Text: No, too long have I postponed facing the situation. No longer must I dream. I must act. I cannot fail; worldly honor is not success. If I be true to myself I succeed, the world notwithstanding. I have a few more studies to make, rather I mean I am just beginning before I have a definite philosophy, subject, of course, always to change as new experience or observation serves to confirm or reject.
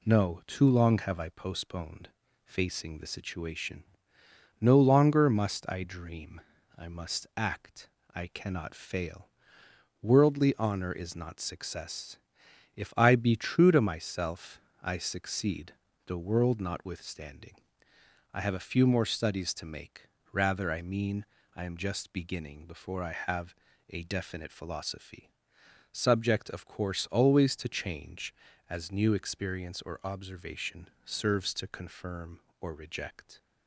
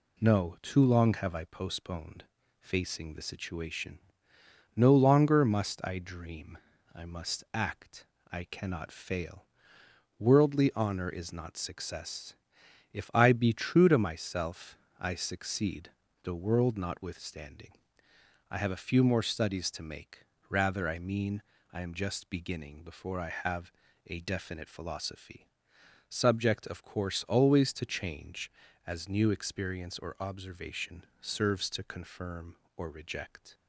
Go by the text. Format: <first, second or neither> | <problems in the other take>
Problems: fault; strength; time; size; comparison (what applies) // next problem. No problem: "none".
neither | pauses between "postponed" and "facing"; slight; the same in both // pauses between "myself" and "I"; slight; the same in both // pauses between "mean" and "I"; slight; the same in both // pauses between "have" and "a"; slight; the same in both // pauses between "observation" and "serves"; slight; the same in both